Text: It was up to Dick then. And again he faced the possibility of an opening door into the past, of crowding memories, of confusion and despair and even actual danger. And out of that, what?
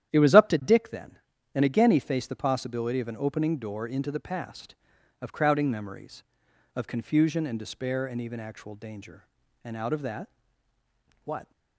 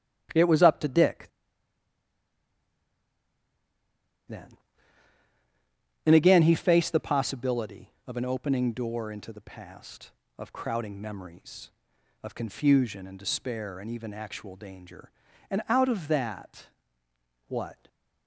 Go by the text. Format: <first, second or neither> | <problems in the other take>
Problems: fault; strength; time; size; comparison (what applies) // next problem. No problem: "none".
first | starts louder than the rest; strong; until 4.3 s; 11 dB; strong in the first // pauses between "Dick" and "then"; strong; at 1.2 s; 3.0 s long